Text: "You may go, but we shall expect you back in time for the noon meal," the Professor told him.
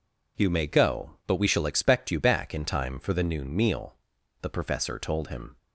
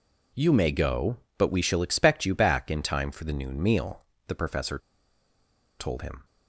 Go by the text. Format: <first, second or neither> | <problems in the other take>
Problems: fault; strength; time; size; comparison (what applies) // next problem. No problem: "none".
first | pauses between "Professor" and "told"; at 4.7 s; 0.99 s long